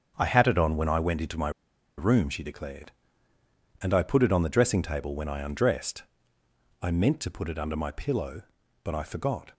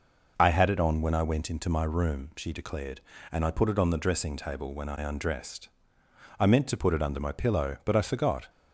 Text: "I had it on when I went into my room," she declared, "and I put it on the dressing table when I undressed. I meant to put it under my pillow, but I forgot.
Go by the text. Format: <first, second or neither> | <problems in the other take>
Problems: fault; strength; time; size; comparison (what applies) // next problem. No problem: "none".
second | starts louder than the rest; until 1.1 s; 7 dB // pauses between "my" and "room"; noticeable; at 1.4 s; 0.48 s long